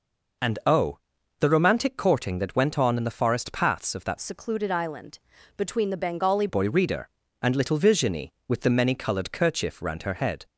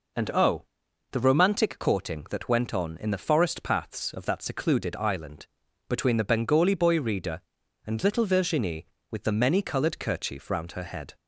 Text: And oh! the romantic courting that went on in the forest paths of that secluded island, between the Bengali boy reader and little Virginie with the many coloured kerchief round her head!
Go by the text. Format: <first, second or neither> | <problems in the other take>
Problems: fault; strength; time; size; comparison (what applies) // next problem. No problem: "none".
second | changes voice from "secluded" to "Bengali"; from 4.1 to 6.4 s; 2.3 s long